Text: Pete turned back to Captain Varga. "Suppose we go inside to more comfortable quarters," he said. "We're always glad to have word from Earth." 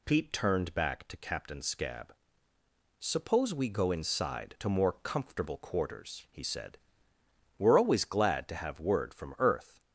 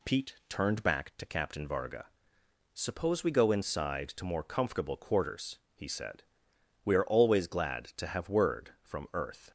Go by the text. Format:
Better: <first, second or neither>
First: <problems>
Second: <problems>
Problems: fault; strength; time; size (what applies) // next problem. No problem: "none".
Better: second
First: says "Scab" for "Varga"; at 1.6 s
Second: none